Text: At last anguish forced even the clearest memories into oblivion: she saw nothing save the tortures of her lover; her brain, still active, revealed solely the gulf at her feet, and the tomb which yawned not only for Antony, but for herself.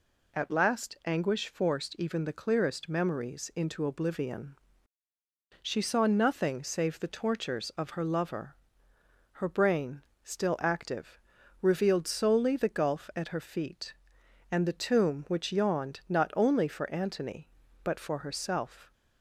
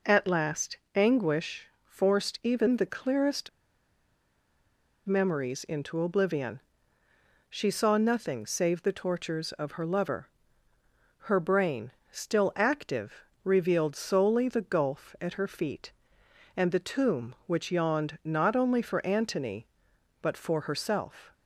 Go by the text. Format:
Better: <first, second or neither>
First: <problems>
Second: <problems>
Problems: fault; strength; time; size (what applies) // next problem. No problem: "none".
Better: first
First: none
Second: pauses between "last" and "anguish"; slight; at 0.7 s; 0.18 s long // pauses between "anguish" and "forced"; slight; at 1.6 s; 0.16 s long // pauses between "clearest" and "memories"; strong; at 3.4 s; 1.5 s long